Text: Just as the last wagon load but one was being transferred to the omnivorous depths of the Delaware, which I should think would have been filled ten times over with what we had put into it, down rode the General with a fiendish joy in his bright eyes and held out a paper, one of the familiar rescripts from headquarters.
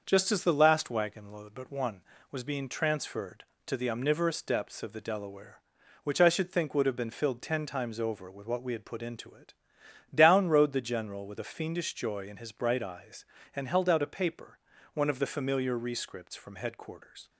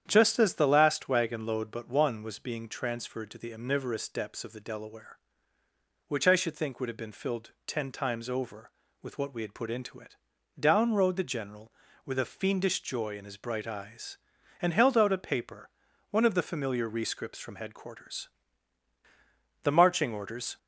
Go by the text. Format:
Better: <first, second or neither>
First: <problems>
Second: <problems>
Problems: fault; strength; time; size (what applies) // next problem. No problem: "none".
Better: first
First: starts louder than the rest; until 1.0 s; 6.5 dB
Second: starts louder than the rest; strong; until 1.0 s; 9 dB // pauses between "filled" and "ten"; slight; at 7.4 s; 0.16 s long // goes on to say "The marching orders"; noticeable; from 19.6 s on; 0.94 s long